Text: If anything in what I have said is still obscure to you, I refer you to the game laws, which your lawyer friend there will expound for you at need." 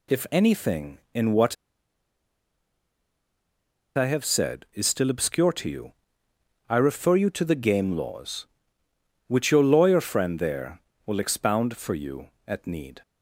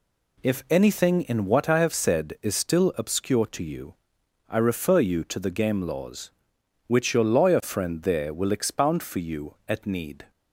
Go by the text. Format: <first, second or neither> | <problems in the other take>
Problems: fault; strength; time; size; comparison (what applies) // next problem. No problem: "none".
second | pauses between "what" and "I"; strong; at 1.5 s; 2.4 s long